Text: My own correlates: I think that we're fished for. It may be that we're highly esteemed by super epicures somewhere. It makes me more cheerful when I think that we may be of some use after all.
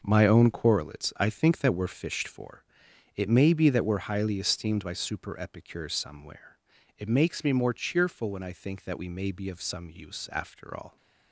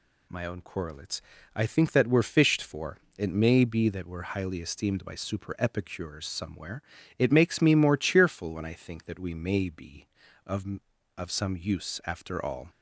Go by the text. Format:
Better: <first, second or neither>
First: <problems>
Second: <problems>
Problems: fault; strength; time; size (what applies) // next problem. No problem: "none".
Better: first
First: none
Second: says "of" twice; at 11.1 s